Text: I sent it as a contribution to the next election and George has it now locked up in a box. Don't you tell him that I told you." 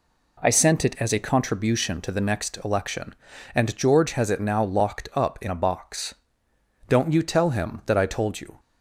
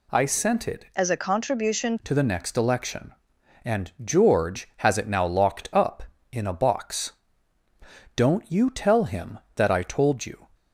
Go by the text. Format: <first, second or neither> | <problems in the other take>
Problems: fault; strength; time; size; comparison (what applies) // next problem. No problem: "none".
first | changes voice from "as" to "contribution"; from 0.9 to 1.9 s; 1.0 s long